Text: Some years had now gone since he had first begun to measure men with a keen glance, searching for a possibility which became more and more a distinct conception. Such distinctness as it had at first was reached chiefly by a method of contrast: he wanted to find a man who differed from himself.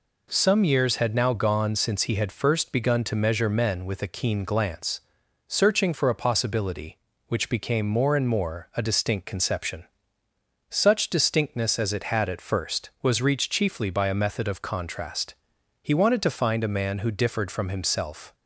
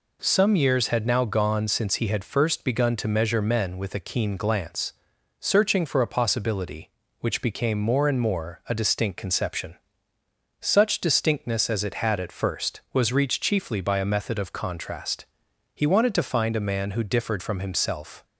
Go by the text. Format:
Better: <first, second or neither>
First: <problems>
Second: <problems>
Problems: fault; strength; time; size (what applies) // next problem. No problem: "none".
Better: neither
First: none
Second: none